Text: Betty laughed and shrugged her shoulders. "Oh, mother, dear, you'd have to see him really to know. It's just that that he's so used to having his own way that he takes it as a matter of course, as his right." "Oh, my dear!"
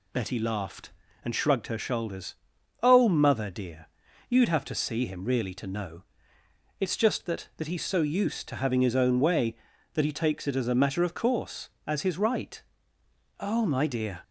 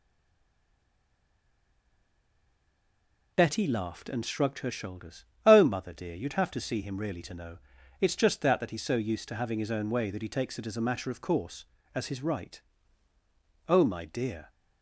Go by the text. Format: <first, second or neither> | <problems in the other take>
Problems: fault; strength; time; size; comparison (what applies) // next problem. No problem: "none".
first | stays silent before the first word; strong; until 3.3 s; 3.3 s long